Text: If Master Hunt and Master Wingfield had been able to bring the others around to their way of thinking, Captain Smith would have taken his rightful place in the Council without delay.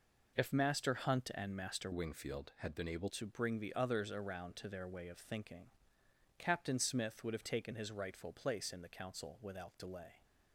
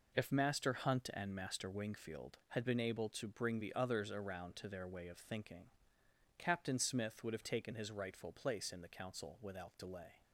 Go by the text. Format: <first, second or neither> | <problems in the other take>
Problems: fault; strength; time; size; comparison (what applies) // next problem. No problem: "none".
second | changes voice from "Wingfield" to "able"; from 1.9 to 3.0 s; 1.1 s long